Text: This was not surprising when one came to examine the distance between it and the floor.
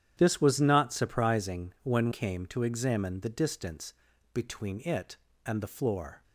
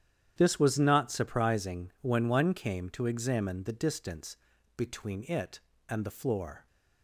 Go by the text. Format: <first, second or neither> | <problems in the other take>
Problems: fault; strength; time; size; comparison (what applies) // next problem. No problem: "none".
second | starts louder than the rest; strong; until 1.1 s; 10 dB; strong in the second // skips "one"; at 2.1 s // pauses between "distance" and "between"; at 3.9 s; 0.40 s long; also in the second